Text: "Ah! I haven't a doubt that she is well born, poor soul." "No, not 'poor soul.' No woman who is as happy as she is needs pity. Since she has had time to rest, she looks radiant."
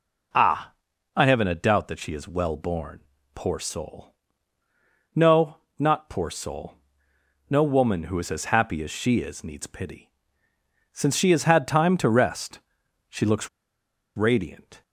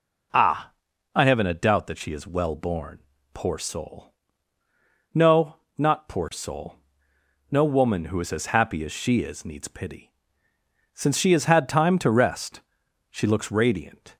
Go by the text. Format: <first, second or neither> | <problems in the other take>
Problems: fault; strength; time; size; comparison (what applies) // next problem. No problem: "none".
second | pauses between "looks" and "radiant"; noticeable; at 13.4 s; 0.67 s long